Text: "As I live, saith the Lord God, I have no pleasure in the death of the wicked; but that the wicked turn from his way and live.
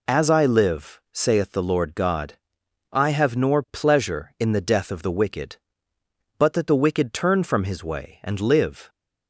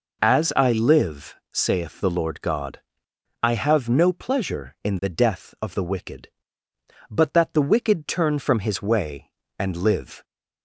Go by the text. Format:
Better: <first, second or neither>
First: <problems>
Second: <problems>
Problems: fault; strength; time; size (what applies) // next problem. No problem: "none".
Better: second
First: says "nor" for "no"; at 3.3 s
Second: none